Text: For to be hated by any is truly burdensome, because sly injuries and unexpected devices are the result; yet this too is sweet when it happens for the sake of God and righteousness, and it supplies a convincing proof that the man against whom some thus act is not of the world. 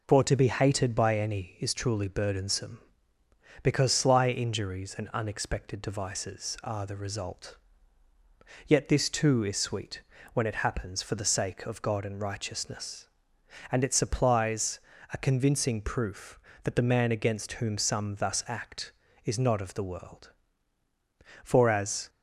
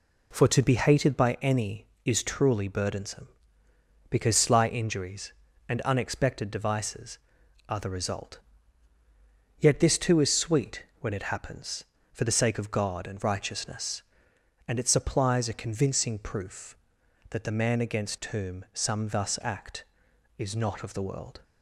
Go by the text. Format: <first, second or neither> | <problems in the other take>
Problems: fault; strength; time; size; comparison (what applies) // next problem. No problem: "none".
second | pauses between "sweet" and "when"; slight; at 10.0 s; 0.32 s long; slight in the second // pauses between "supplies" and "a"; slight; at 14.7 s; 0.36 s long // goes on to say "For as"; noticeable; from 21.4 s on; 0.64 s long